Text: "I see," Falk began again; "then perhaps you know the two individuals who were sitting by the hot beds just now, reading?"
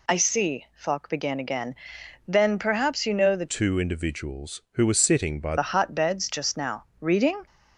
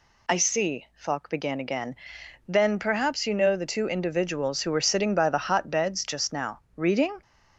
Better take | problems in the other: second | changes voice from "two" to "by"; from 3.4 to 5.5 s; 2.1 s long

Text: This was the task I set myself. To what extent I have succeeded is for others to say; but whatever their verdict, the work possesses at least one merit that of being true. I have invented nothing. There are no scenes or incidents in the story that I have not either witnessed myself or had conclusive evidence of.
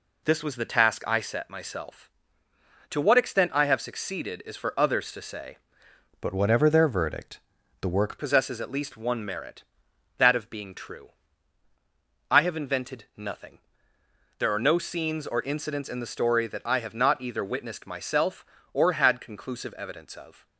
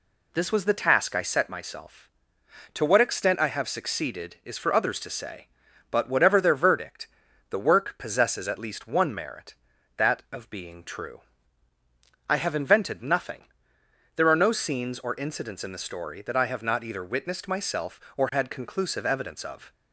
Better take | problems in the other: second | changes voice from "but" to "work"; from 6.2 to 8.1 s; 1.9 s long

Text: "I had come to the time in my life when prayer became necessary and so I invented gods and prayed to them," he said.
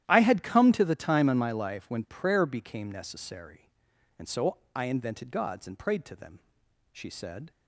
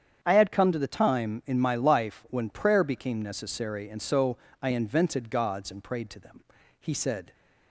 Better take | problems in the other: second | starts louder than the rest; strong; until 1.0 s; 12 dB; strong in the second // pauses between "so" and "I"; slight; at 4.5 s; 0.18 s long; slight in the second // says "she" for "he"; at 6.9 s

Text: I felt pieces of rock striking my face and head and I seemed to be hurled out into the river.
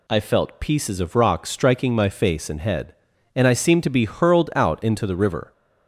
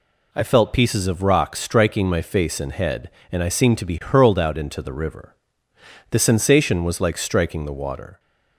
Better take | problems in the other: first | goes on to say "The sensation was like striking the water"; strong; from 6.0 s on; 2.1 s long

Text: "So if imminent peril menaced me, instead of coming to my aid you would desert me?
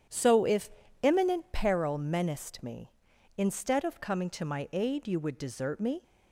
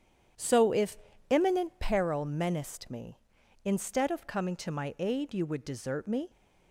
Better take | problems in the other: neither | starts louder than the rest; strong; the same in both // pauses between "if" and "imminent"; slight; the same in both

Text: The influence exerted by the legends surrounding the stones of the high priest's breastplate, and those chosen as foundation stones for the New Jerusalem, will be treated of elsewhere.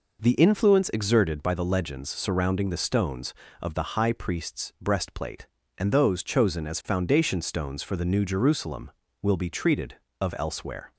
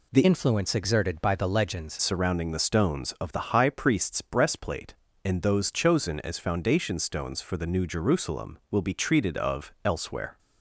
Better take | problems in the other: first | changes voice from "influence" to "legends"; from 0.2 to 1.9 s; 1.7 s long

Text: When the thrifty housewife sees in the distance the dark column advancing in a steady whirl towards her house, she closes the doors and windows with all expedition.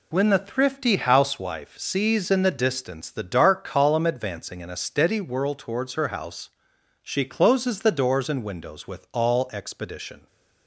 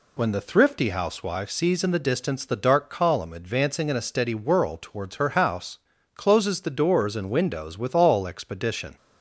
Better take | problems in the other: first | skips "she"; at 5.9 s

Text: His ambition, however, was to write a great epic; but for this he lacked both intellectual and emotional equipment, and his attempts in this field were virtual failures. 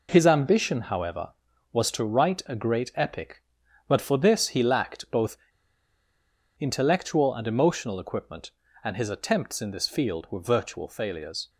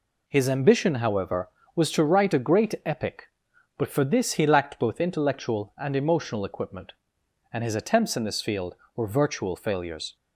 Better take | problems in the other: second | pauses between "both" and "intellectual"; at 5.3 s; 1.2 s long

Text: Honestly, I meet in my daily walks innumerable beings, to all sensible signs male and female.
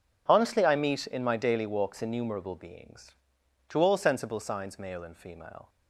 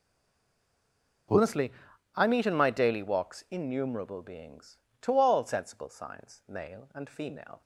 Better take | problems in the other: first | stays silent before the first word; noticeable; until 1.2 s; 1.2 s long

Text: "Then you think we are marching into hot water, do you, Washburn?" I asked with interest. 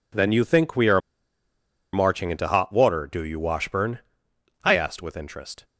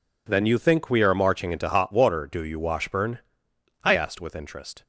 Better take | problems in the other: second | pauses between "are" and "marching"; noticeable; at 0.9 s; 0.93 s long

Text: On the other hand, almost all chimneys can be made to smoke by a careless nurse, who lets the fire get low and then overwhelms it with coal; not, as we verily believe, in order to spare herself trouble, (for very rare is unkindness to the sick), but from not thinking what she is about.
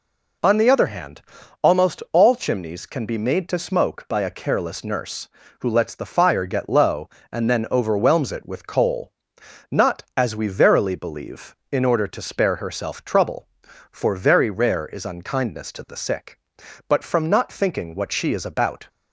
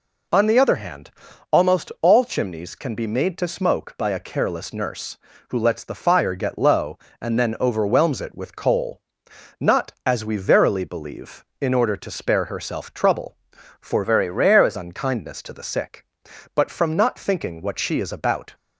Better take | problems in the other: first | changes voice from "very" to "is"; from 14.0 to 14.7 s; 0.7 s long

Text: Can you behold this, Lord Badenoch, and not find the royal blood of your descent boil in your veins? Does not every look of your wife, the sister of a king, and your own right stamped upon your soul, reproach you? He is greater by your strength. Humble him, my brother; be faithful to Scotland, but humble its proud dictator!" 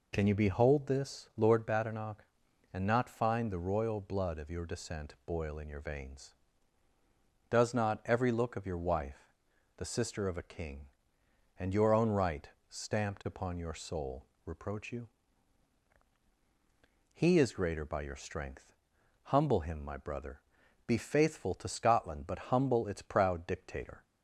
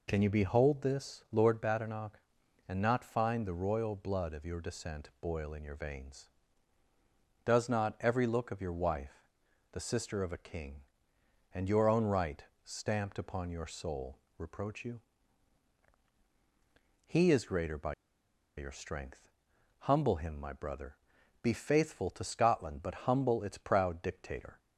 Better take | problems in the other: first | pauses between "right" and "stamped"; slight; at 12.4 s; 0.24 s long; slight in the first // pauses between "by" and "your"; noticeable; at 17.9 s; 0.64 s long

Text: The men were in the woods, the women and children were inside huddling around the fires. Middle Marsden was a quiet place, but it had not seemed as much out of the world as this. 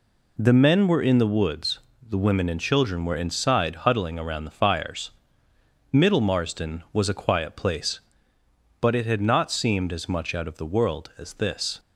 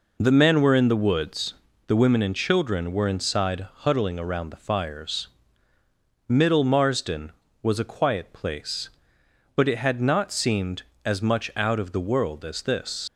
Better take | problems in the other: first | leaves "this" unfinished; at 13.0 s; 60 ms

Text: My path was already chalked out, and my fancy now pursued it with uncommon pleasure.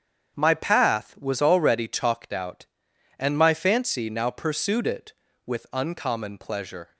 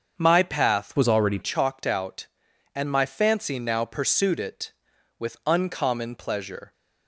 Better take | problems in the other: first | starts louder than the rest; until 1.2 s; 7 dB; strong in the first // changes voice from "was" to "already"; from 0.9 to 1.3 s; 0.4 s long

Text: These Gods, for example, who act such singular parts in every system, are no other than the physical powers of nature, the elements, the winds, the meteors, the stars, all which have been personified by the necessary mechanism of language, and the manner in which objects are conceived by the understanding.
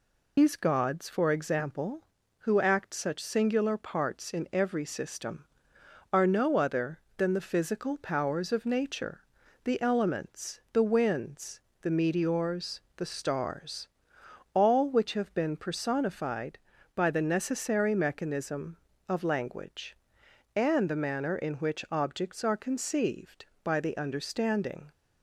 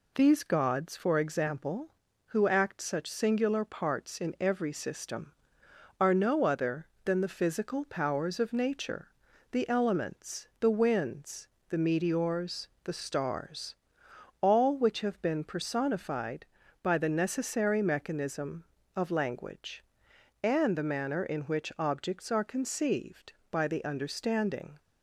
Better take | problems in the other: second | loses the start of "These"; at 0.3 s; 105 ms

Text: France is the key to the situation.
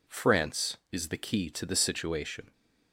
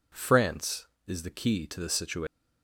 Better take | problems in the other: neither | none

